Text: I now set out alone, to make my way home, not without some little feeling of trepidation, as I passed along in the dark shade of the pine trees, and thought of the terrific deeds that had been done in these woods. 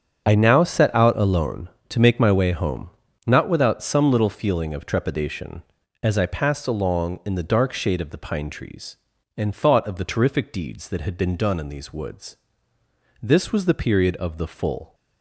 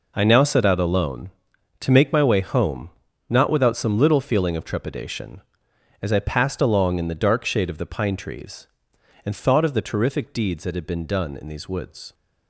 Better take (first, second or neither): second